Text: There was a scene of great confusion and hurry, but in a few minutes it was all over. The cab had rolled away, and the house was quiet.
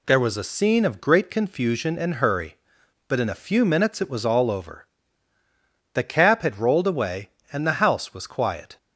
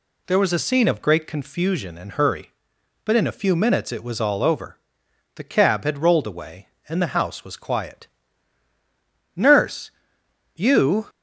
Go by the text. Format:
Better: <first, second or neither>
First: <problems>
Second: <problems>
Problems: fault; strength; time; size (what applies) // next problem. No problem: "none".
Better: first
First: none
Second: goes on to say "Nurse you"; strong; from 9.3 s on; 1.7 s long